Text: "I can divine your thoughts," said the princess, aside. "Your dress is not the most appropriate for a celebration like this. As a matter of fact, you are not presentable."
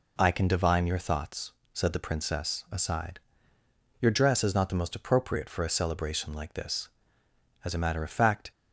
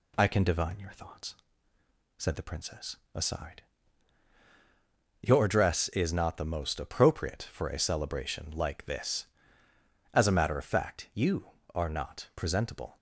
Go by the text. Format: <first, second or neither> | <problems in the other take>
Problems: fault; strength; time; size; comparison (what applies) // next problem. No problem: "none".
second | stops before "you are not presentable"; at 8.5 s